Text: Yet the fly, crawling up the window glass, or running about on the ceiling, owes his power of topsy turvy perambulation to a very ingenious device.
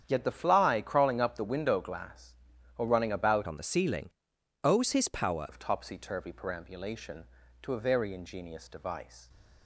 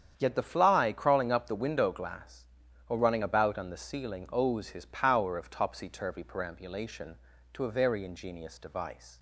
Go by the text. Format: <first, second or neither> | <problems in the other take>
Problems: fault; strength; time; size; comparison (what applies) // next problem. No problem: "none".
second | starts louder than the rest; strong; until 1.0 s; 9 dB; strong in the second // changes voice from "on" to "power"; from 3.4 to 5.4 s; 2.0 s long